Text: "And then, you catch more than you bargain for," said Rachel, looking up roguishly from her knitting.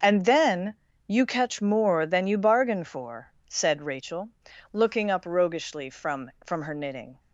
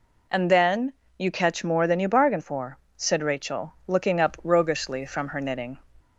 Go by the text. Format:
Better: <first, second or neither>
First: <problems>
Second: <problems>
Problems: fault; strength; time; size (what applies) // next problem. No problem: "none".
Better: second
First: says "from" twice; at 6.4 s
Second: none